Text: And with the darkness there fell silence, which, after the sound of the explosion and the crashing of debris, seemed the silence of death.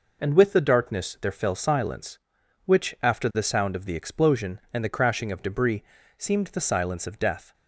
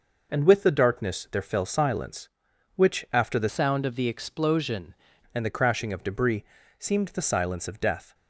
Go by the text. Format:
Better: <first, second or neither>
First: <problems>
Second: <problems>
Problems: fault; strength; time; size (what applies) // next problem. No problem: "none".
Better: first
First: none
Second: changes voice from "sound" to "explosion"; from 3.4 to 4.9 s; 1.5 s long